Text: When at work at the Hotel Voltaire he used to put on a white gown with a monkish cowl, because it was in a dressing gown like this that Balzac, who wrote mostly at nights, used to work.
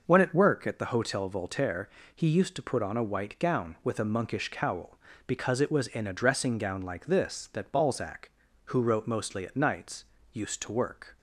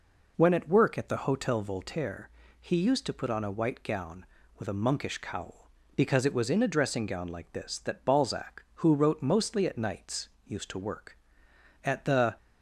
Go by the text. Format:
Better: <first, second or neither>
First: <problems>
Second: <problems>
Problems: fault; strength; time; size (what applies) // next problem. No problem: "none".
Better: first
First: pauses between "Voltaire" and "he"; slight; at 1.8 s; 0.26 s long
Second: pauses between "Voltaire" and "he"; slight; at 2.2 s; 0.30 s long // goes on to say "At the"; from 11.8 s on; 0.52 s long